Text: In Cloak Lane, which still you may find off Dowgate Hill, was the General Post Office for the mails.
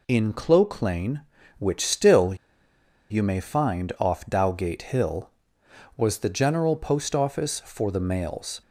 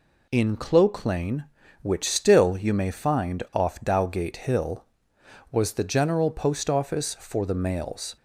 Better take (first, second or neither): second